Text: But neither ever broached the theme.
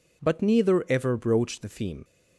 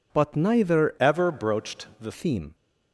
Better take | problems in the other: first | changes voice from "ever" to "the"; from 0.9 to 2.1 s; 1.2 s long

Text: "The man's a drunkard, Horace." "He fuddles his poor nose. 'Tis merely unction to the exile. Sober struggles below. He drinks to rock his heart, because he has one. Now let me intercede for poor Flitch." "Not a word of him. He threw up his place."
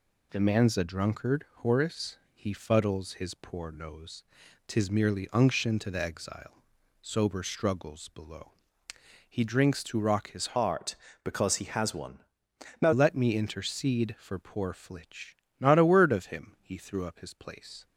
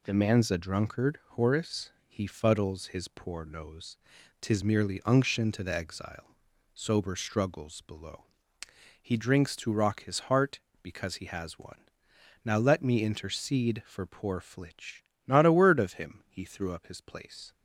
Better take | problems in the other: second | changes voice from "heart" to "Now"; from 10.5 to 12.9 s; 2.4 s long

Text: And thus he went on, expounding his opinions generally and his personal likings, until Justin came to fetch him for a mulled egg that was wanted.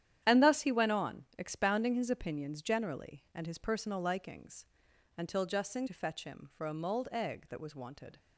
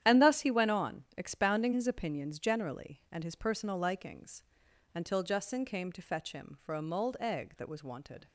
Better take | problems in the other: second | starts louder than the rest; strong; until 1.2 s; 10.5 dB; strong in the second // skips "came"; at 5.8 s

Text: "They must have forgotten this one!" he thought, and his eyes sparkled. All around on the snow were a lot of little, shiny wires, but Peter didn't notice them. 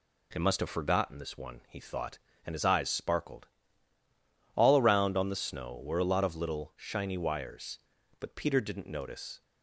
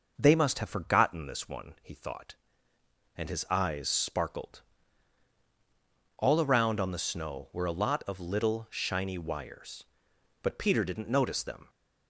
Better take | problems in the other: second | stops before "them"; at 9.4 s

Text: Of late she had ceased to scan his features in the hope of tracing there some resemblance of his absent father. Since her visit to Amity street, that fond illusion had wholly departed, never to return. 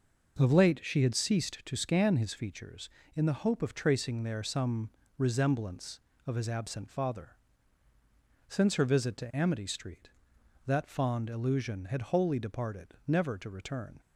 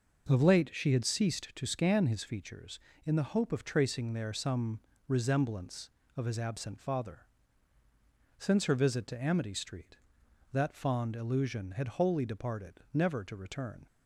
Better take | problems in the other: neither | pauses between "some" and "resemblance"; slight; the same in both

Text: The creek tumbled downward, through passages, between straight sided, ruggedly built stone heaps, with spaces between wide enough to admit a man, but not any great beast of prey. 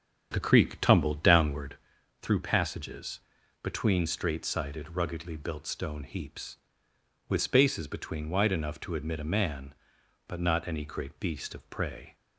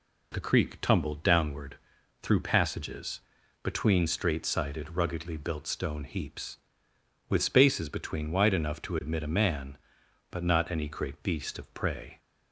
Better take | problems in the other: second | starts louder than the rest; strong; until 1.9 s; 7.5 dB

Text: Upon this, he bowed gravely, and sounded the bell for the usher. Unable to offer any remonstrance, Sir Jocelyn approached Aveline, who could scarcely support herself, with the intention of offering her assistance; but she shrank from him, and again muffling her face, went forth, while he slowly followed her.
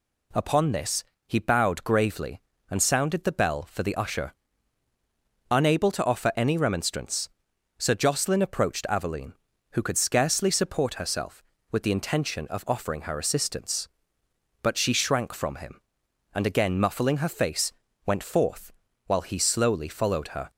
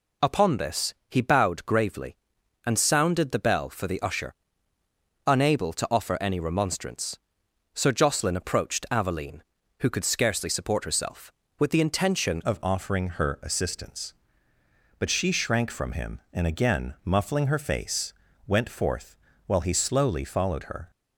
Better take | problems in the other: first | changes voice at "of"; from 12.4 s on; 8.5 s long

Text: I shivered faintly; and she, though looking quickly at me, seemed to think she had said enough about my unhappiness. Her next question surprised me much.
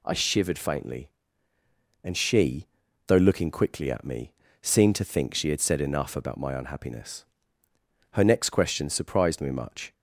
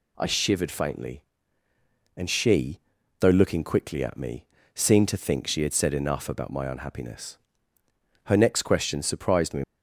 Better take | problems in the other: first | stops before "much"; at 9.6 s

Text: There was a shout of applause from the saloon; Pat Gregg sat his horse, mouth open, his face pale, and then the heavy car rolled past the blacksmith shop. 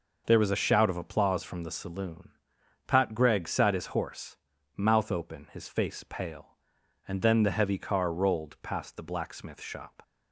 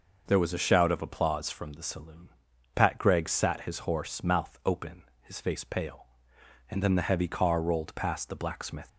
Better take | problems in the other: first | stops before "shop"; at 8.8 s

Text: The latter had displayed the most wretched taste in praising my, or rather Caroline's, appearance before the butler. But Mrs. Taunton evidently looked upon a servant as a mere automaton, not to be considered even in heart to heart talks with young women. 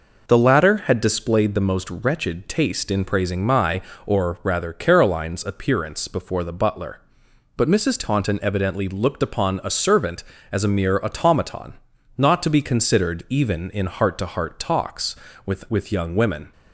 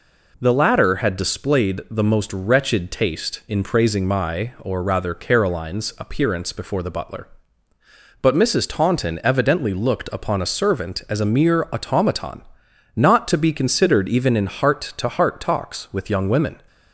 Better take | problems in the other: second | says "with" twice; at 15.6 s

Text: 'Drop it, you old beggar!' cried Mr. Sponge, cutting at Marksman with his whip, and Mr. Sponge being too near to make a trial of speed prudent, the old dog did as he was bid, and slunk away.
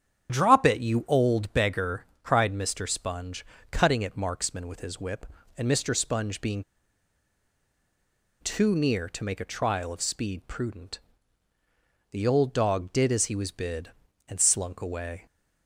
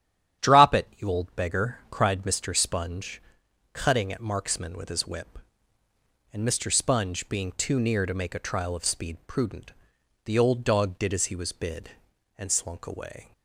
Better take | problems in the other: second | starts louder than the rest; strong; until 1.3 s; 8.5 dB; strong in the second // pauses between "being" and "too"; strong; at 6.6 s; 1.7 s long

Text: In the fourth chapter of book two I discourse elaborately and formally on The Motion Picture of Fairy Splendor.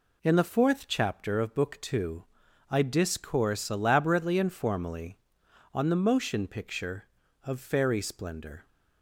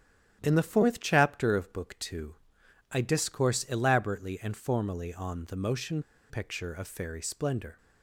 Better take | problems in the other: first | starts louder than the rest; strong; until 1.4 s; 11 dB // pauses between "two" and "I"; noticeable; at 2.3 s; 0.58 s long; also in the first // pauses between "Motion" and "Picture"; slight; at 6.0 s; 0.28 s long

